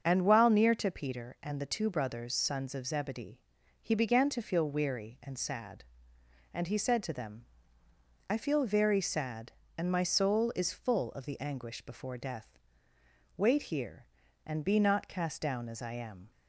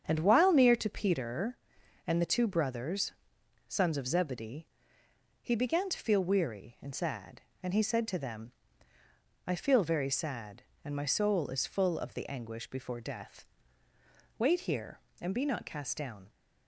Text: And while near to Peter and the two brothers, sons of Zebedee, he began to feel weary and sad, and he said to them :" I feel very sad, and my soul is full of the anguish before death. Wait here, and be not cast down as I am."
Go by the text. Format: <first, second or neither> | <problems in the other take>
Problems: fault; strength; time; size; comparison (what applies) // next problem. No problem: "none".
first | starts louder than the rest; strong; until 1.0 s; 8 dB; strong in the first // stops before "as I am"; at 16.2 s